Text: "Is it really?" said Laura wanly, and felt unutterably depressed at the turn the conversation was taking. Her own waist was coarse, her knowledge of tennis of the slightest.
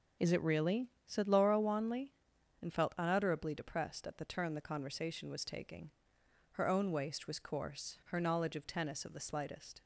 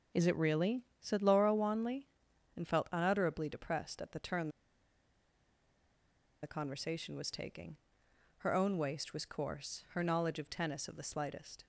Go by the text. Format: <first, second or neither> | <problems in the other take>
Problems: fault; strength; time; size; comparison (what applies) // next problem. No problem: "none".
first | starts louder than the rest; until 1.3 s; 6.5 dB; also in the first // pauses between "turn" and "the"; strong; at 4.4 s; 1.9 s long